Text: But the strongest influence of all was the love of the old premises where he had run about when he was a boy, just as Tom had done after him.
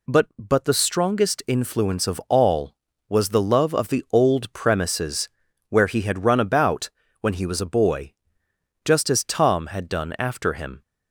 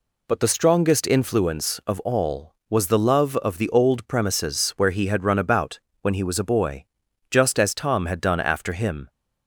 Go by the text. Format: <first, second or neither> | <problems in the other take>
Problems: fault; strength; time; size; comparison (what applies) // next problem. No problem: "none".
second | says "But" twice; at 0.3 s // pauses between "premises" and "where"; at 5.2 s; 0.40 s long // pauses between "about" and "when"; slight; at 6.9 s; 0.32 s long; slight in the second